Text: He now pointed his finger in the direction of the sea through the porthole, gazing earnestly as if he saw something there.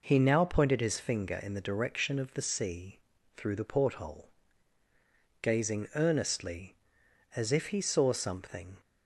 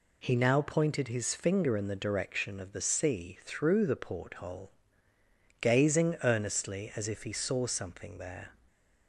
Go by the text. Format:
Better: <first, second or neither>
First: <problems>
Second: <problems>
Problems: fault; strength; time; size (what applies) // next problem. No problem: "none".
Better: second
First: pauses between "sea" and "through"; at 2.9 s; 0.40 s long // stops before "there"; at 8.8 s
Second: none